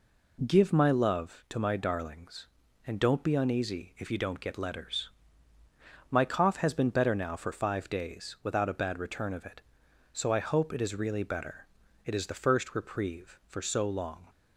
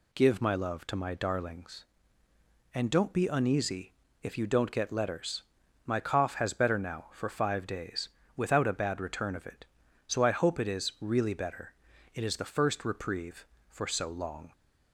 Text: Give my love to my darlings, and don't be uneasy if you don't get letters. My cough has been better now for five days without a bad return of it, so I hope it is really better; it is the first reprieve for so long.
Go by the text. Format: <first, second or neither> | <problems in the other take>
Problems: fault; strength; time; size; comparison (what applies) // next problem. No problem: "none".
first | pauses between "uneasy" and "if"; slight; at 3.9 s; 0.28 s long // skips "been"; at 6.5 s // pauses between "days" and "without"; slight; at 8.0 s; 0.26 s long